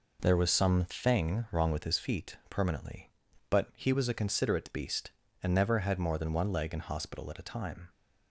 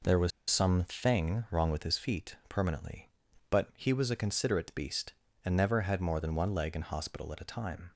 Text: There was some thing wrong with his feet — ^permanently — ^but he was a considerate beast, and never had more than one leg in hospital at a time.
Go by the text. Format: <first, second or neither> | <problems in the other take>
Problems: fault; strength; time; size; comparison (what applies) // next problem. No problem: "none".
first | pauses between "was" and "some"; slight; at 0.3 s; 0.19 s long